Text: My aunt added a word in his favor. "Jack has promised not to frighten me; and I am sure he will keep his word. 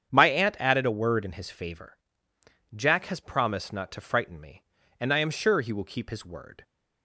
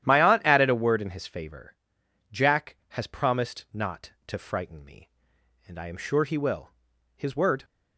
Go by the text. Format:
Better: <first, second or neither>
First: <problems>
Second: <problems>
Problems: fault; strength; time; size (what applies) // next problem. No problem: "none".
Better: first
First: starts louder than the rest; strong; until 1.1 s; 8 dB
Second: starts louder than the rest; strong; until 1.1 s; 11 dB // skips "keep"; at 6.9 s